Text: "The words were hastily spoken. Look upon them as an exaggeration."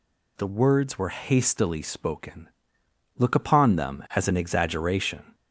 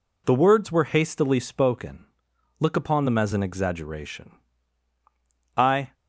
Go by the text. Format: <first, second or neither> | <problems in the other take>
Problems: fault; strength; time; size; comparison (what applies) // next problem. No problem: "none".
first | goes on to say "I"; slight; from 5.5 s on; 0.36 s long